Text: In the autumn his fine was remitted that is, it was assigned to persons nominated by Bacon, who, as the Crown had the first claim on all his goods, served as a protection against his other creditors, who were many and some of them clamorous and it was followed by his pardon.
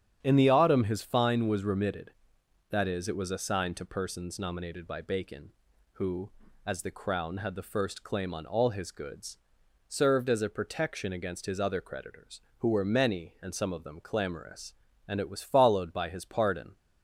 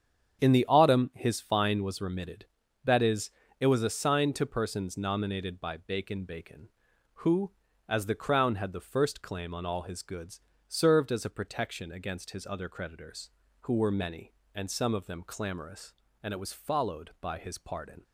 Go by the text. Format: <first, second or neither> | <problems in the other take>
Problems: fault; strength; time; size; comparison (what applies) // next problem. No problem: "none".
first | starts louder than the rest; strong; until 1.4 s; 8.5 dB; strong in the first // says "Bacon" twice; at 6.2 s